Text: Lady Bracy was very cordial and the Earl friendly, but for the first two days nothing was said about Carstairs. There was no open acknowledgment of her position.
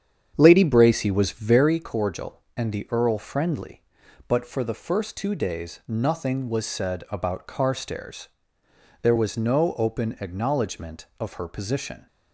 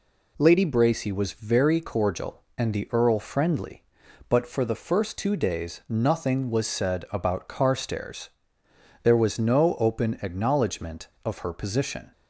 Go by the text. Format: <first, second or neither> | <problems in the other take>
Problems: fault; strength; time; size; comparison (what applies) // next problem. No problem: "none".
second | starts louder than the rest; strong; until 1.8 s; 8 dB